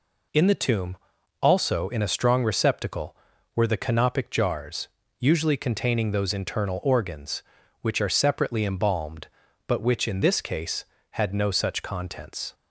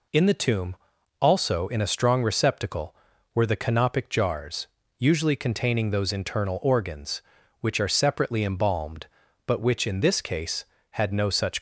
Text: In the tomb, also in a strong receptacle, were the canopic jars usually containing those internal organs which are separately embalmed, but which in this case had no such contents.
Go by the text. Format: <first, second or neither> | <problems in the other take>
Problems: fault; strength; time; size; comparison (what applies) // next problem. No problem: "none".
first | pauses between "jars" and "usually"; slight; at 4.6 s; 0.32 s long; slight in the first // stops before "contents"; at 11.5 s